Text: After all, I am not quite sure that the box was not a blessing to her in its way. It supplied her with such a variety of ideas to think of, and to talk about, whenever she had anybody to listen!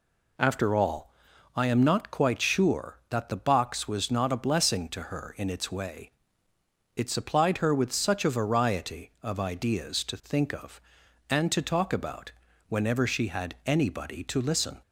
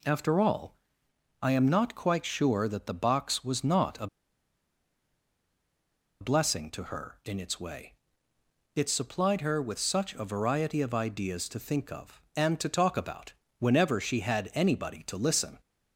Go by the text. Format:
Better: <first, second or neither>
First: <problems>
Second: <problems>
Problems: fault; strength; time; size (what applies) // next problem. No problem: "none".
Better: first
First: none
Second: pauses between "a" and "blessing"; strong; at 4.0 s; 2.1 s long